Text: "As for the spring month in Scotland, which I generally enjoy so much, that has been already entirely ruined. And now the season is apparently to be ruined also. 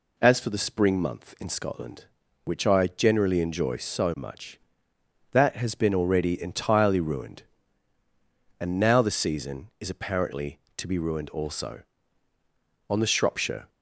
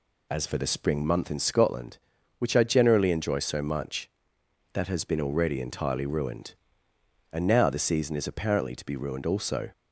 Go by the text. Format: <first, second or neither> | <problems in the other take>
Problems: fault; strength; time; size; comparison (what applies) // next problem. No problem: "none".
second | goes on to say "On the Shropshire"; noticeable; from 12.8 s on; 0.80 s long